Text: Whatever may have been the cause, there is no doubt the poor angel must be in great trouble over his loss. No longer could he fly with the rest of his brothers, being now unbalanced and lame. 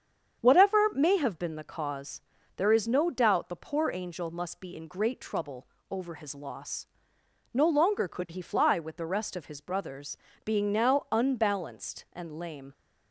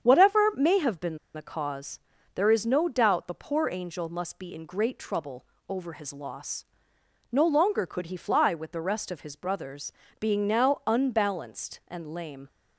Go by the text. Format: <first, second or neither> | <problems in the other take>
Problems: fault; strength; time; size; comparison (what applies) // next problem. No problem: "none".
first | starts louder than the rest; strong; until 1.0 s; 8 dB; strong in the first // pauses between "been" and "the"; slight; at 1.1 s; 0.17 s long // pauses between "trouble" and "over"; slight; at 5.4 s; 0.22 s long; slight in the first